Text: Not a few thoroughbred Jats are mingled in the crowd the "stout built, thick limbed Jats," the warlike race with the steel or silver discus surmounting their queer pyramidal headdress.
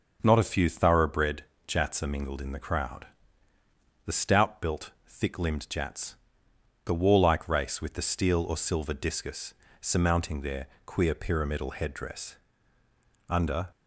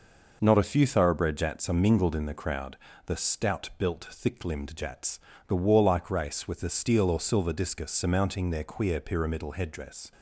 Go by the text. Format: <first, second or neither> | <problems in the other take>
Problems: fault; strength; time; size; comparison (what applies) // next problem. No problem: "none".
second | starts louder than the rest; until 1.2 s; 6.5 dB // pauses between "thoroughbred" and "Jats"; slight; at 1.4 s; 0.22 s long // pauses between "crowd" and "the"; noticeable; at 3.0 s; 0.98 s long; slight in the second // pauses between "discus" and "surmounting"; slight; at 9.5 s; 0.26 s long // pauses between "their" and "queer"; slight; at 10.6 s; 0.18 s long // goes on to say "Under"; slight; from 13.3 s on; 0.40 s long